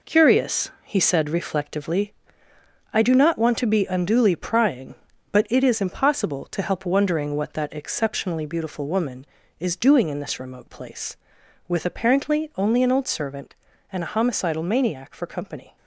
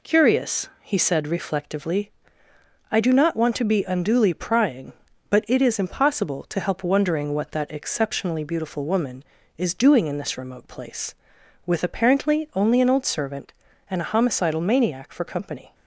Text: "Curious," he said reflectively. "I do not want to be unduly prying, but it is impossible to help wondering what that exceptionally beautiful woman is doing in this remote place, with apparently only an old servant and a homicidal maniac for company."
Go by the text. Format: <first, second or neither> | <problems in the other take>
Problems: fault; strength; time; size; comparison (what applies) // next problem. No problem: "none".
second | gets quieter; throughout; 6.5 dB